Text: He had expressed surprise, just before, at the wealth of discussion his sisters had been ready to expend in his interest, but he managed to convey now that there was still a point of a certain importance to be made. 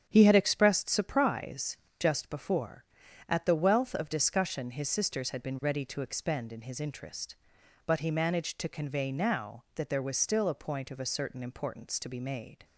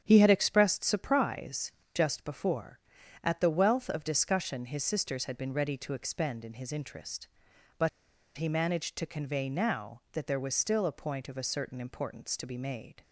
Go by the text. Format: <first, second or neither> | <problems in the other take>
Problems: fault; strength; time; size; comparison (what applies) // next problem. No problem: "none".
first | starts louder than the rest; strong; until 1.0 s; 8 dB; strong in the first // pauses between "but" and "he"; noticeable; at 7.8 s; 0.48 s long